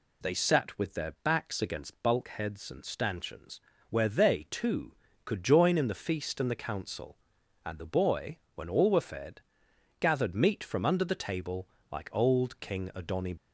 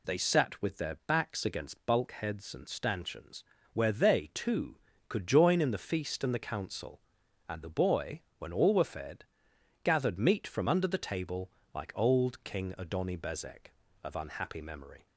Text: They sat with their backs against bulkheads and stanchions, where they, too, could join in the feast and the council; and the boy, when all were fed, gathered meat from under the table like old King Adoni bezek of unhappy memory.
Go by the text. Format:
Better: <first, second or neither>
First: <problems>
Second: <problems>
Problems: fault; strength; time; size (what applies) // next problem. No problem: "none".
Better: second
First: pauses between "table" and "like"; slight; at 11.6 s; 0.24 s long // stops before "bezek of unhappy memory"; at 13.3 s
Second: pauses between "table" and "like"; slight; at 11.4 s; 0.24 s long